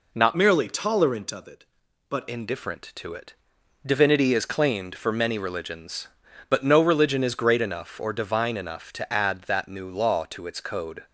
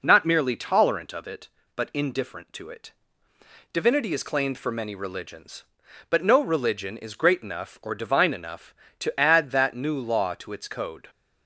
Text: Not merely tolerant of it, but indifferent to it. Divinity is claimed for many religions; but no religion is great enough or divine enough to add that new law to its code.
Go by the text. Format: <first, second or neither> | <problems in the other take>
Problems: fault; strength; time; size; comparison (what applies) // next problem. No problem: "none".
second | changes voice from "merely" to "but"; from 0.3 to 2.2 s; 1.9 s long